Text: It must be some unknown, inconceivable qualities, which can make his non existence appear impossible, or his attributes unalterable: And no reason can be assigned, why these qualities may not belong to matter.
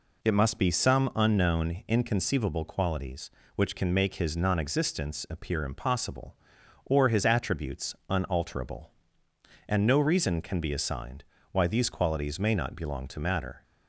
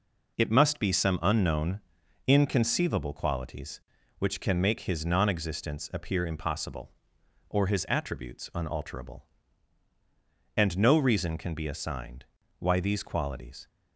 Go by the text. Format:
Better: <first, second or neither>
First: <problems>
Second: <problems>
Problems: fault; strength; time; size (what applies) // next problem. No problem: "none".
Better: first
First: none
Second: stops before "may not belong to matter"; at 13.6 s